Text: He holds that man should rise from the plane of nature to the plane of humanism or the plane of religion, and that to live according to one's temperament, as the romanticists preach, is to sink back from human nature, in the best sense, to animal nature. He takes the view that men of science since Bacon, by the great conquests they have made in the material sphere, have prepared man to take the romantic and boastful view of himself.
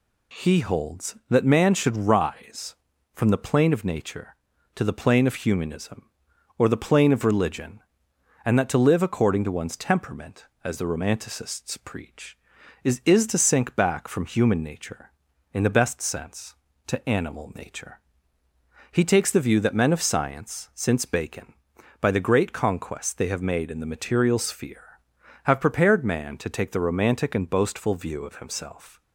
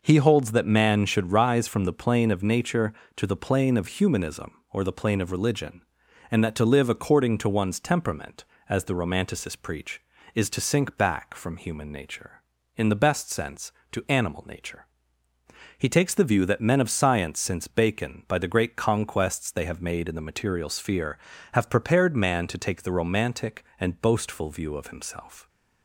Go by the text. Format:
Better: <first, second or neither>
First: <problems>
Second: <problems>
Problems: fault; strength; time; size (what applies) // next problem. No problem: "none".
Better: second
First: says "is" twice; at 13.0 s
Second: none